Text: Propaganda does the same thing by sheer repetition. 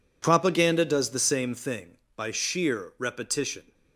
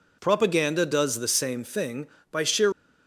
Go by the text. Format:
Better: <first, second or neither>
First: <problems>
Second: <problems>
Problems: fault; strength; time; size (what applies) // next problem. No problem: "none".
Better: first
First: none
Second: stops before "repetition"; at 2.7 s